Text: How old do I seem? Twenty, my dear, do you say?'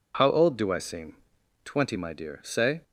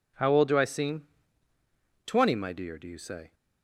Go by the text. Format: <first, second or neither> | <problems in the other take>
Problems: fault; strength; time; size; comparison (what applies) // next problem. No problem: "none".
second | skips "do you"; at 2.4 s